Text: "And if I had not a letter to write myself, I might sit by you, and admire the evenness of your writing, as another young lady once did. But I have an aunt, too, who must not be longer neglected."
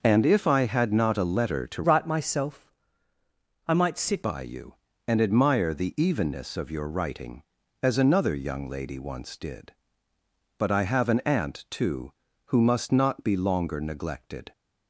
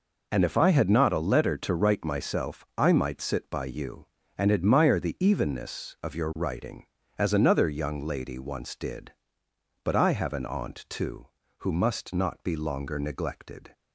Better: second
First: starts louder than the rest; noticeable; until 1.0 s; 6 dB // changes voice from "write" to "sit"; from 1.8 to 4.2 s; 2.4 s long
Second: none

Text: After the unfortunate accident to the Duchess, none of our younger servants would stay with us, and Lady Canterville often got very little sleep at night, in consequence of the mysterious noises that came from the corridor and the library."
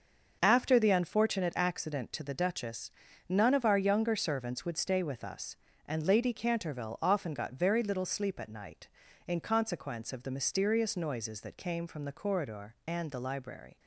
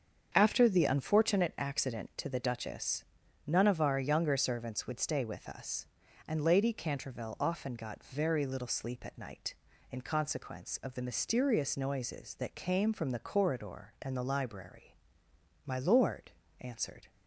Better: first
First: starts louder than the rest; until 1.4 s; 6.5 dB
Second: starts louder than the rest; strong; until 1.3 s; 7.5 dB // goes on to say "My Lord answered"; from 15.6 s on; 1.4 s long

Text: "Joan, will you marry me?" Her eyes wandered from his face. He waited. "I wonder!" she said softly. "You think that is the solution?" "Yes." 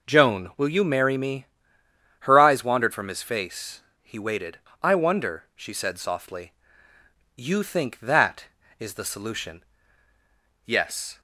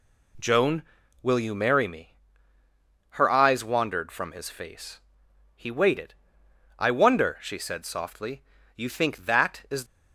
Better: first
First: none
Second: stops before "the solution Yes"; at 9.8 s

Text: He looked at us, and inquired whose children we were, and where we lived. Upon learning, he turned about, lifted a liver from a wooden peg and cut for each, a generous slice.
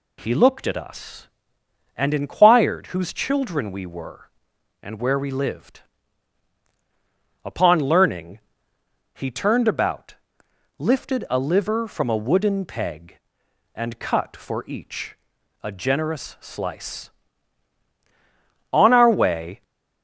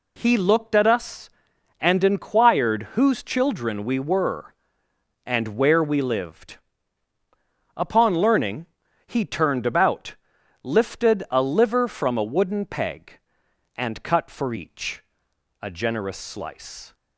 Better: second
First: goes on to say "On our way"; noticeable; from 18.7 s on; 0.90 s long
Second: none

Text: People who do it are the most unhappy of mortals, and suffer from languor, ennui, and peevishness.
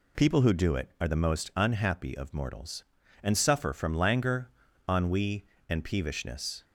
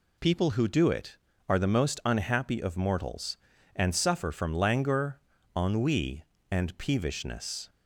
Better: neither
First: none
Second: none

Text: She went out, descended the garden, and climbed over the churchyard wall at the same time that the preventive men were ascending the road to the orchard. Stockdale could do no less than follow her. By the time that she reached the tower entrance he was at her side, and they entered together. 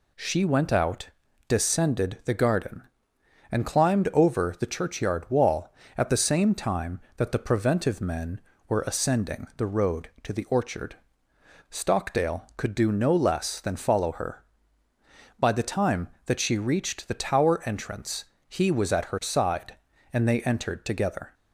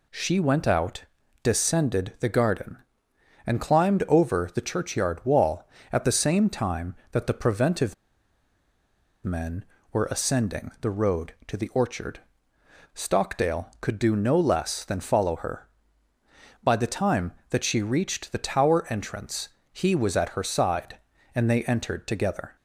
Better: first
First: pauses between "entrance" and "he"; slight; at 18.2 s; 0.22 s long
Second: pauses between "preventive" and "men"; strong; at 7.9 s; 1.2 s long // pauses between "entrance" and "he"; slight; at 19.4 s; 0.22 s long

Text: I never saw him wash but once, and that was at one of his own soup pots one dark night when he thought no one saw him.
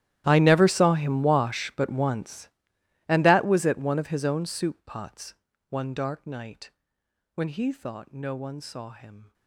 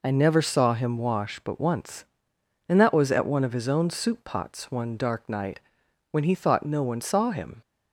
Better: second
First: gets quieter; strong; throughout; 22.5 dB // pauses between "pots" and "one"; slight; at 5.3 s; 0.34 s long // pauses between "night" and "when"; noticeable; at 6.7 s; 0.64 s long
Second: pauses between "night" and "when"; noticeable; at 5.5 s; 0.52 s long

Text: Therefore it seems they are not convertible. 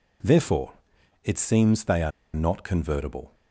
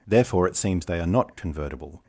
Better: second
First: pauses between "Therefore" and "it"; noticeable; at 0.7 s; 0.50 s long // pauses between "are" and "not"; slight; at 2.1 s; 0.22 s long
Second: none

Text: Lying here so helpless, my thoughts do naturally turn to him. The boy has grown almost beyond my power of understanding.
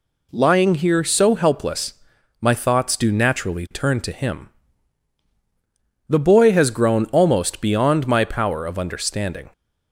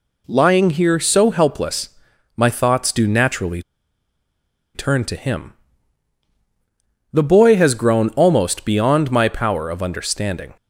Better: first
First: none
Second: pauses between "naturally" and "turn"; at 3.6 s; 1.1 s long

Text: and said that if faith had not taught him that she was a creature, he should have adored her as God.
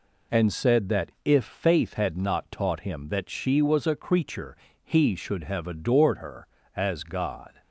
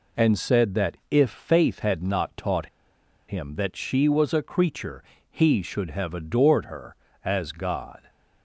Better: first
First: none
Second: pauses between "taught" and "him"; noticeable; at 2.6 s; 0.61 s long

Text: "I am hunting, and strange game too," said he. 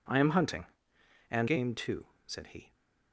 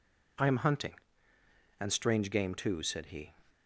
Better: second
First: skips "strange"; at 1.4 s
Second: none

